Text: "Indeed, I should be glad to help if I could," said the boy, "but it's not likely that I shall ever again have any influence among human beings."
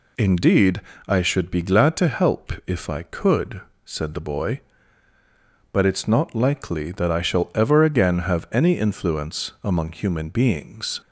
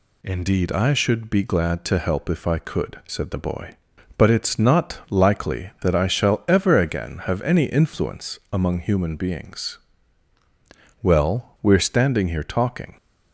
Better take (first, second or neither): first